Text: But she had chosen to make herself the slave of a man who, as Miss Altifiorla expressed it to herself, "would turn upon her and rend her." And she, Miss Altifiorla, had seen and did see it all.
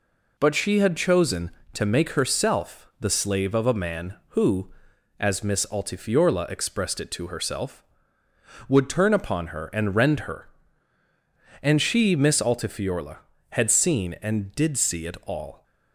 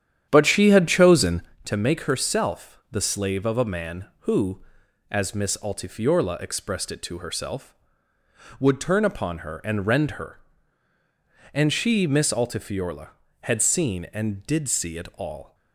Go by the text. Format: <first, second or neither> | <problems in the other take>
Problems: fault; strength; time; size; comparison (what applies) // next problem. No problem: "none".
first | starts louder than the rest; strong; until 1.6 s; 10 dB